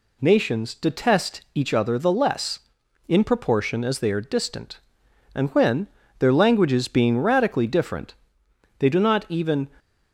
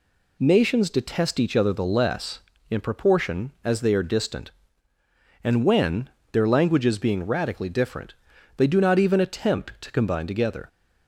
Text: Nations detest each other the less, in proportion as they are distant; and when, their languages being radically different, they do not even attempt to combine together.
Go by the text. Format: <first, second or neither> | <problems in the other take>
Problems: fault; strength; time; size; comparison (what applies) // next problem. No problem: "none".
second | stops before "attempt to combine together"; at 9.7 s